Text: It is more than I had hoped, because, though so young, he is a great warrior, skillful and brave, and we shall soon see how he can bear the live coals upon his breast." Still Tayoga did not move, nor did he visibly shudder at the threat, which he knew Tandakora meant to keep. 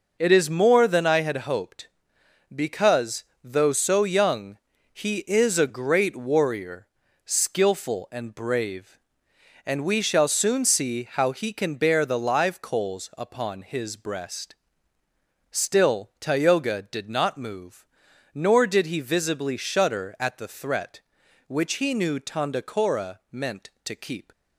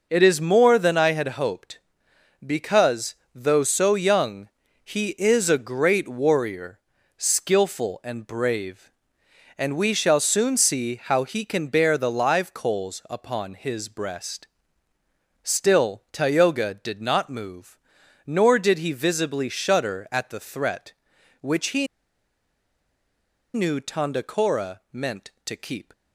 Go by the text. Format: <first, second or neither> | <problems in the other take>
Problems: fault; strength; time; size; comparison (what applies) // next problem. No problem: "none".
first | pauses between "he" and "knew"; strong; at 21.8 s; 1.6 s long